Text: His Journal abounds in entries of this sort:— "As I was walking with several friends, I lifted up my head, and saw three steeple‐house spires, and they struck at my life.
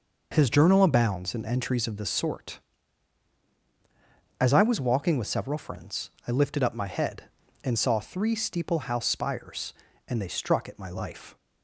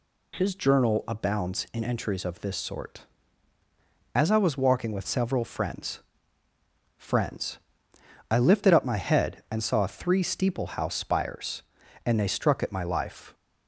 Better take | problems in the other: first | says "friends" twice; at 6.9 s

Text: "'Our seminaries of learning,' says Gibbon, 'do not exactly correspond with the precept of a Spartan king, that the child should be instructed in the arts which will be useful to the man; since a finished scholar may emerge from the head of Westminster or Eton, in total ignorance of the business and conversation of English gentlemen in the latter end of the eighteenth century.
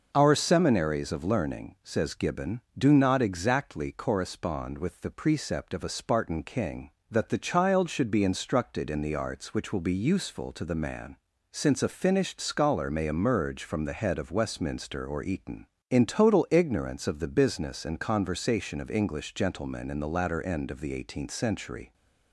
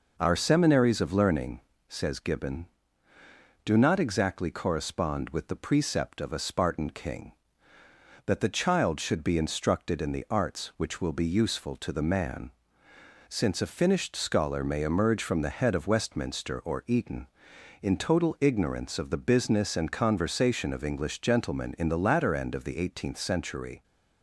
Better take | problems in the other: neither | none

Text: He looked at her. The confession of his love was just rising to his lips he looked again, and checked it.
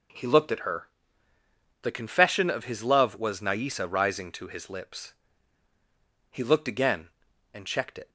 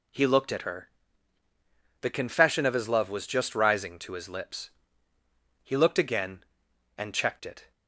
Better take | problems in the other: second | says "naisa" for "just"; at 3.4 s // pauses between "lips" and "he"; at 5.1 s; 1.1 s long; noticeable in the second

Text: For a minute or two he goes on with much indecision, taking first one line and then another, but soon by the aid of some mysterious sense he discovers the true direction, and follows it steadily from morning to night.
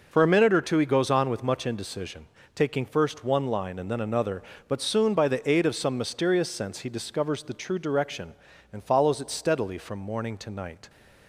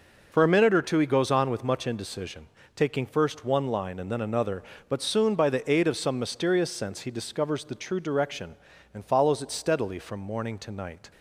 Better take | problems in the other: neither | none

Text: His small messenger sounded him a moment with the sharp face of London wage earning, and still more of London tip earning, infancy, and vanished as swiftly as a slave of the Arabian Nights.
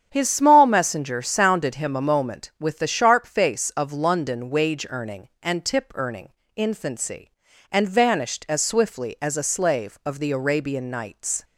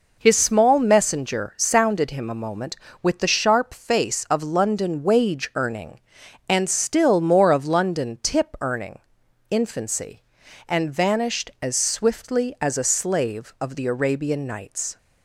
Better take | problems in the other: second | starts louder than the rest; strong; until 1.1 s; 8.5 dB // skips "still more of London"; at 5.6 s

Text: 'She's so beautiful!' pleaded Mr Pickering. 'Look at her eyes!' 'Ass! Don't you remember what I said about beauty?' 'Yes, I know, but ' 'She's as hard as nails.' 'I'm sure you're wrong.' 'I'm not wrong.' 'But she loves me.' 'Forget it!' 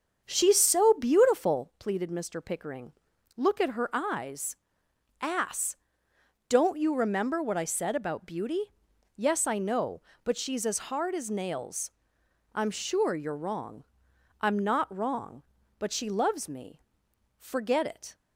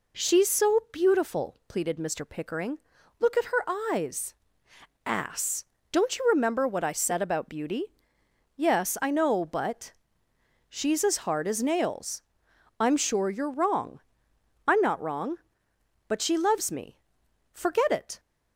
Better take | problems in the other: second | starts louder than the rest; strong; until 1.7 s; 7.5 dB

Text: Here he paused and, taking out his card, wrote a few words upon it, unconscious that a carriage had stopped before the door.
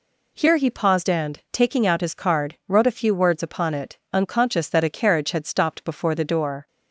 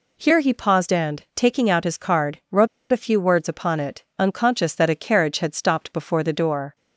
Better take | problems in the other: first | pauses between "wrote" and "a"; slight; at 2.6 s; 0.25 s long

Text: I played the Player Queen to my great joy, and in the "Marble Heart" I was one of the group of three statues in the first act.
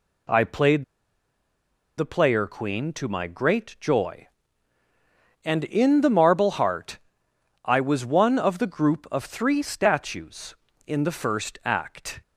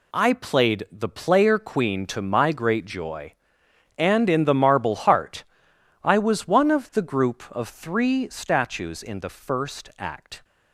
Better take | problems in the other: second | pauses between "played" and "the"; at 0.8 s; 1.1 s long // pauses between "Heart" and "I"; noticeable; at 6.9 s; 0.64 s long; noticeable in the second

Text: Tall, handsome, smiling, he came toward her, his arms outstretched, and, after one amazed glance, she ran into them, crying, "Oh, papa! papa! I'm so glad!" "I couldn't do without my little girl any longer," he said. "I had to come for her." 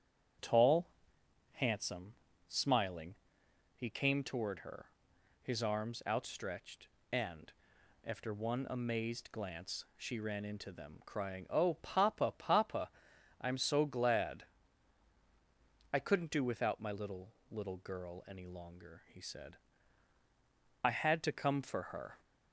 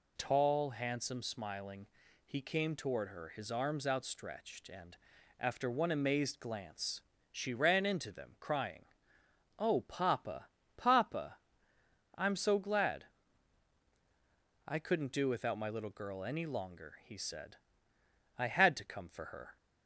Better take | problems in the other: second | starts louder than the rest; strong; until 2.0 s; 8 dB // says "little" twice; at 17.4 s

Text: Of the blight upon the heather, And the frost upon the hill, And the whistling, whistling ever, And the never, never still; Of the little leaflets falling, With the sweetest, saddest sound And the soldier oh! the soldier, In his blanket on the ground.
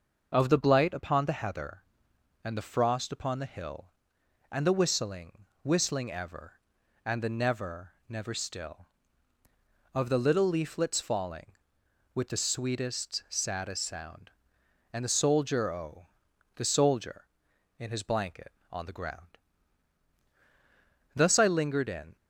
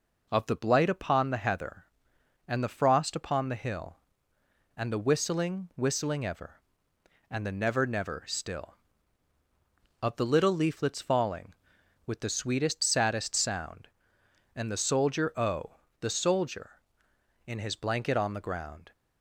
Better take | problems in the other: second | starts louder than the rest; noticeable; until 1.3 s; 6 dB // goes on to say "Thus I lingered in"; noticeable; from 21.1 s on; 1.0 s long

